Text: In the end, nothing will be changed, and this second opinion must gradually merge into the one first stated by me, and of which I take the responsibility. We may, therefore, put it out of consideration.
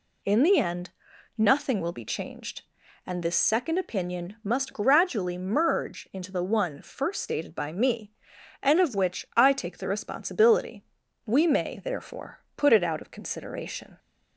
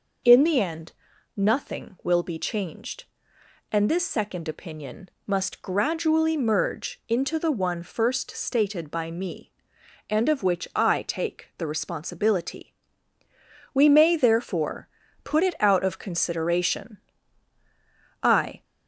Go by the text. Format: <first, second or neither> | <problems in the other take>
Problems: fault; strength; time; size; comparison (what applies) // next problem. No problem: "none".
first | pauses between "opinion" and "must"; slight; at 5.0 s; 0.18 s long // goes on to say "I"; slight; from 18.2 s on; 0.42 s long